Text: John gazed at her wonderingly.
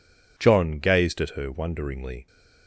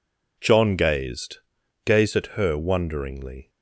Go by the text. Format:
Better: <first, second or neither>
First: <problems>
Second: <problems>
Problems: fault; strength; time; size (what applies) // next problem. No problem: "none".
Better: first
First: none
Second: says "gazed" twice; at 1.8 s